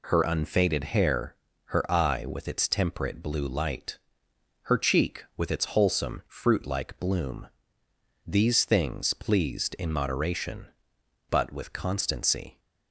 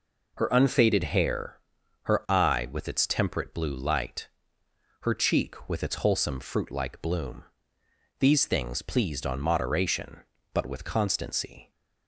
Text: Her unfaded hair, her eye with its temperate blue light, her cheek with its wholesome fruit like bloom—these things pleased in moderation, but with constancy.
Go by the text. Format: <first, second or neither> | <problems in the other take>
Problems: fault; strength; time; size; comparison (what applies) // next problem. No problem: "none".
first | says "on" for "in"; at 9.2 s